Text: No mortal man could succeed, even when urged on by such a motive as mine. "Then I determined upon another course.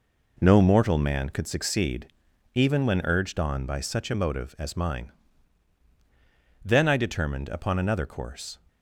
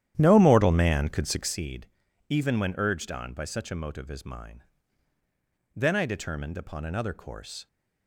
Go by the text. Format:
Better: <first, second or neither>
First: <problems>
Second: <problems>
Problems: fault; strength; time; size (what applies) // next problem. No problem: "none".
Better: first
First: none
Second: starts louder than the rest; strong; until 1.6 s; 11 dB